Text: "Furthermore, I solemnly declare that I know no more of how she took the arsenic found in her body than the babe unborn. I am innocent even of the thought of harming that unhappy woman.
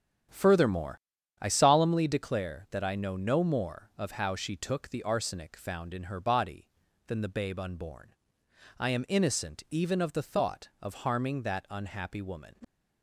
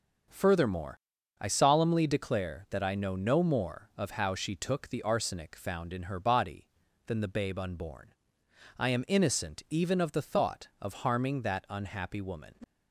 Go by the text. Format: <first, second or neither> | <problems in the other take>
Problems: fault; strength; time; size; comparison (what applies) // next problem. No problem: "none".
second | starts louder than the rest; strong; until 1.9 s; 9 dB